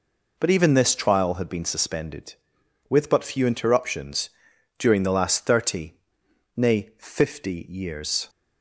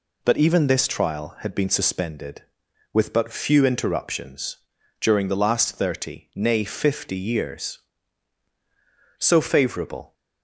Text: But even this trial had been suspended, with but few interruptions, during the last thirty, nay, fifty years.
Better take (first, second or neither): first